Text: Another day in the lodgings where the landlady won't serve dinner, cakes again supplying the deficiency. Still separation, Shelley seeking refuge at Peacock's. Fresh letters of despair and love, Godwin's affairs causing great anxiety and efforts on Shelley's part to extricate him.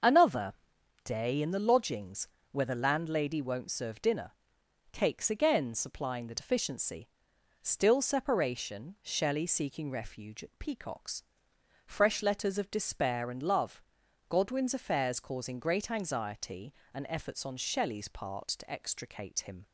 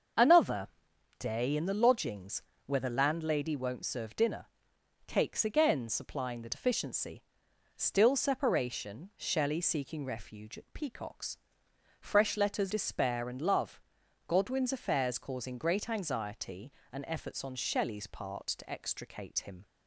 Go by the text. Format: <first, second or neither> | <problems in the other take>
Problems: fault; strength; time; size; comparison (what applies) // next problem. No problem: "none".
first | starts louder than the rest; until 1.6 s; 6.5 dB; also in the first // pauses between "Another" and "day"; noticeable; at 0.6 s; 0.52 s long; noticeable in the first // pauses between "lodgings" and "where"; slight; at 2.4 s; 0.24 s long; slight in the first // skips "of"; at 12.7 s